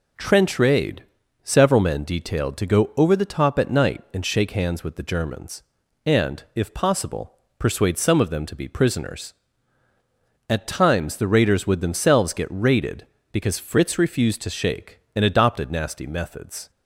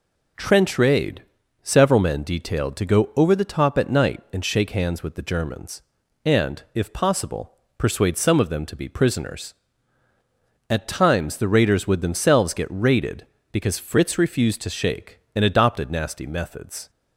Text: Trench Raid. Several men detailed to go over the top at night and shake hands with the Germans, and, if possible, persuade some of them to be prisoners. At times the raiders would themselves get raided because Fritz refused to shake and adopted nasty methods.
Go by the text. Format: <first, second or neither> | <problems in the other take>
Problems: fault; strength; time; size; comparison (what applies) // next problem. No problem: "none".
neither | none